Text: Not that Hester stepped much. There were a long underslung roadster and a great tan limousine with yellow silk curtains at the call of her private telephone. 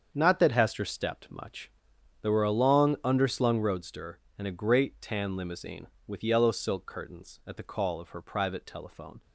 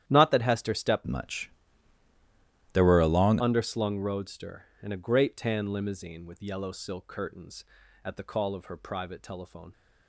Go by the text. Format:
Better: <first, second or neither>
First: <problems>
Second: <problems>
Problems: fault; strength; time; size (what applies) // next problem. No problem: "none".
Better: first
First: starts louder than the rest; strong; until 1.1 s; 7 dB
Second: starts louder than the rest; strong; until 1.1 s; 11 dB // changes voice from "much" to "long"; from 1.0 to 3.3 s; 2.3 s long